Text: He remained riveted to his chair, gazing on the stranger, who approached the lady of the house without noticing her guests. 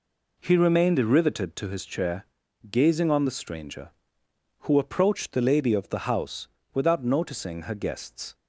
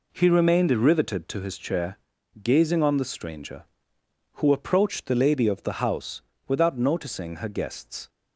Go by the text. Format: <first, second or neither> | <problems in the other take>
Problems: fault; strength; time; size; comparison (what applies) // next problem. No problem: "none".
neither | pauses between "house" and "without"; slight; the same in both